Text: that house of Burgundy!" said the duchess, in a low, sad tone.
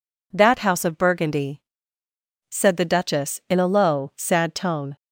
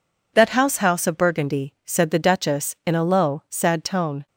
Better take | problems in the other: first | says "house" twice; at 0.7 s

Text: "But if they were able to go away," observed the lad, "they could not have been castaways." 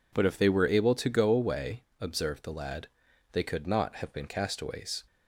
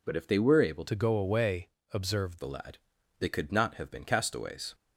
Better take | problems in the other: first | changes voice from "to" to "observed"; from 0.8 to 2.3 s; 1.5 s long

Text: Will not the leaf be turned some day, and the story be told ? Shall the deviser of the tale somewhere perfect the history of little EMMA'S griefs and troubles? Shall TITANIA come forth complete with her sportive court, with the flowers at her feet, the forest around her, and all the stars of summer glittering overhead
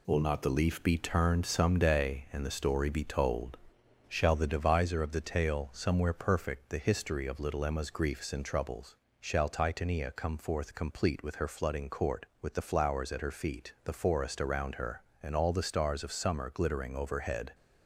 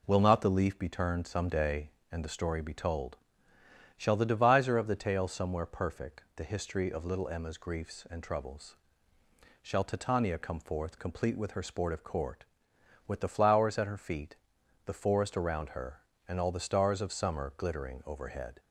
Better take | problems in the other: second | says "flooding" for "sportive"; at 11.4 s

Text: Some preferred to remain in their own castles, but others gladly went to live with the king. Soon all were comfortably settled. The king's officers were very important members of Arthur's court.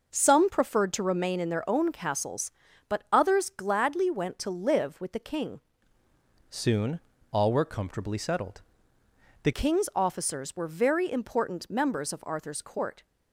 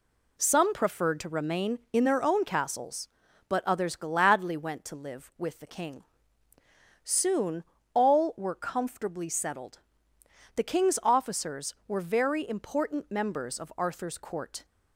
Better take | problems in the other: second | changes voice from "Soon" to "The"; from 6.4 to 9.5 s; 3.1 s long // pauses between "Soon" and "all"; slight; at 6.9 s; 0.32 s long; slight in the second

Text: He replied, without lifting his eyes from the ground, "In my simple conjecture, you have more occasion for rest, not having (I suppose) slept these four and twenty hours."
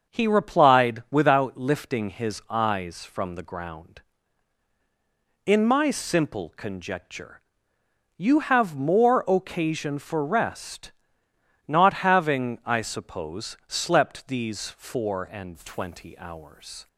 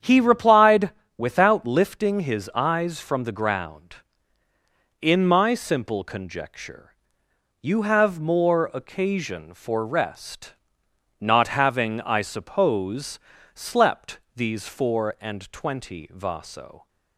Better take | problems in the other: first | starts louder than the rest; strong; until 1.2 s; 8.5 dB; also in the first // says "vaso" for "hours"; at 16.0 s

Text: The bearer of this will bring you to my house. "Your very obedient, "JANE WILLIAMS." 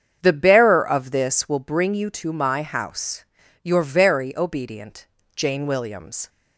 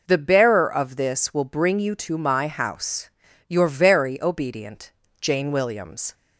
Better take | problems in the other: second | starts louder than the rest; strong; until 1.6 s; 7.5 dB

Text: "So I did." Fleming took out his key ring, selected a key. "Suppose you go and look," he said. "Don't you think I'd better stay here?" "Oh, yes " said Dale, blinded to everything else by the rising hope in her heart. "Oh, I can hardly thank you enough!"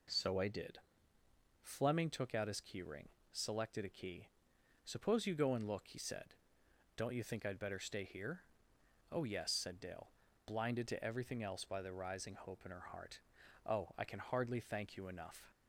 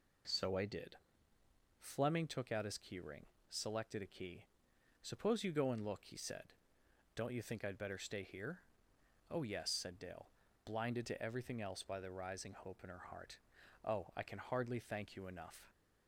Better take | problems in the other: neither | none

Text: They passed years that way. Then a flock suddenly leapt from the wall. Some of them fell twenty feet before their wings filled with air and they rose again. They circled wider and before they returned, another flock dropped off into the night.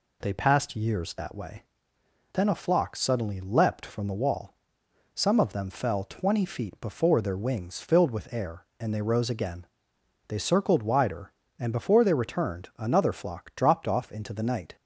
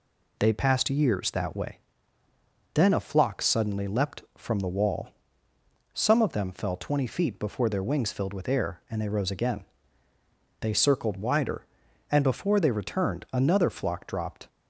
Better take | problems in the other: first | stops before "off into the night"; at 14.4 s

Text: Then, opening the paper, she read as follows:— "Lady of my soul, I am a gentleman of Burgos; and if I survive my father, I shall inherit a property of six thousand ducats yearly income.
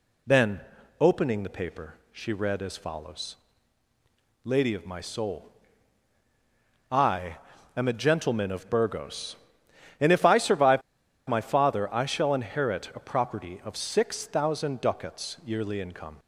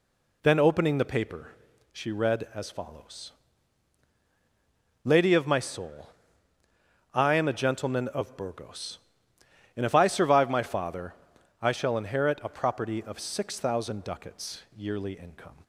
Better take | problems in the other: second | pauses between "I" and "am"; at 7.3 s; 0.40 s long // pauses between "survive" and "my"; noticeable; at 10.8 s; 0.46 s long

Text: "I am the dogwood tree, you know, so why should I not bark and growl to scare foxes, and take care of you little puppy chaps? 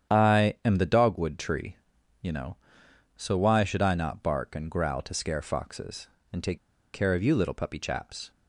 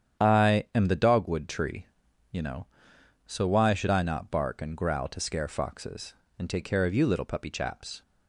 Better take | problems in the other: second | starts louder than the rest; strong; until 1.2 s; 9 dB; strong in the second // pauses between "take" and "care"; slight; at 6.5 s; 0.35 s long

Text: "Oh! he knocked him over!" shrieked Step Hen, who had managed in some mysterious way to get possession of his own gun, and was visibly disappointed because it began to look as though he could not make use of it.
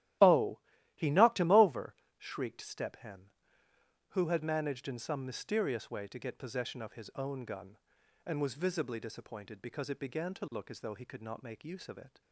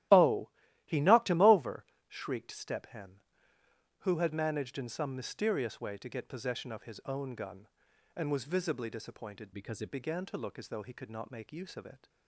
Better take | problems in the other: first | starts louder than the rest; strong; until 1.5 s; 14.5 dB; strong in the first // changes voice from "because" to "it"; from 9.5 to 9.9 s; 0.4 s long

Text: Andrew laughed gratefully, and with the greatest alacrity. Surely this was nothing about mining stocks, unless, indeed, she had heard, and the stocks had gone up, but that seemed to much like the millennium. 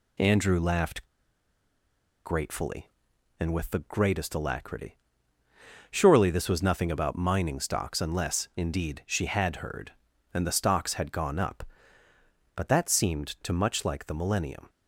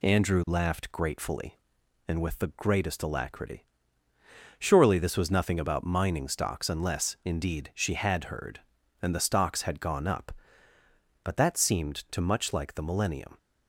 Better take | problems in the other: second | pauses between "laughed" and "gratefully"; at 1.0 s; 1.2 s long

